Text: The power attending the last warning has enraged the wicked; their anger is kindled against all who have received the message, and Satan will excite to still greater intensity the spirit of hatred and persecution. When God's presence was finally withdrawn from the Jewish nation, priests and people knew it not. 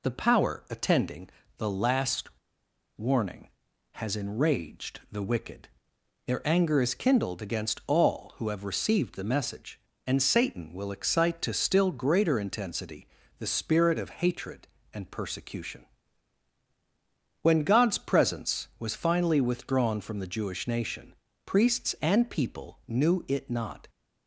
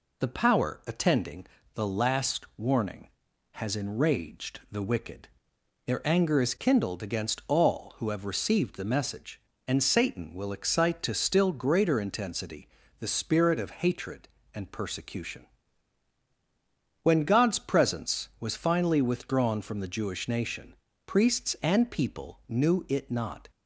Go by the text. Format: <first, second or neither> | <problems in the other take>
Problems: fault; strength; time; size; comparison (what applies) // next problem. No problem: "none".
second | pauses between "attending" and "the"; slight; at 1.2 s; 0.30 s long; slight in the second // pauses between "last" and "warning"; noticeable; at 2.2 s; 0.69 s long // pauses between "intensity" and "the"; slight; at 13.0 s; 0.32 s long; slight in the second